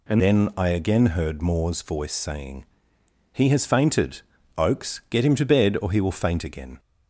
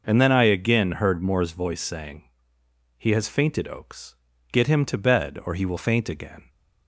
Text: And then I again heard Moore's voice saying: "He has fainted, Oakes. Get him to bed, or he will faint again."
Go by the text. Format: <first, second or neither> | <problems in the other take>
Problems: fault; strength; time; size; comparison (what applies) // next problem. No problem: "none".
second | changes voice at "then"; from 0.1 s on; 6.6 s long